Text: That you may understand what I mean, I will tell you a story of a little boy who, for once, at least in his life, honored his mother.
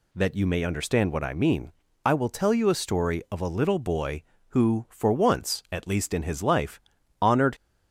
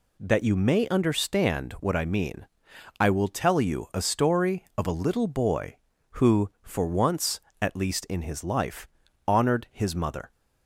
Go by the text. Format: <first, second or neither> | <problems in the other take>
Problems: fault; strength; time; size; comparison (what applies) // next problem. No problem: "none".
second | stops before "his mother"; at 7.5 s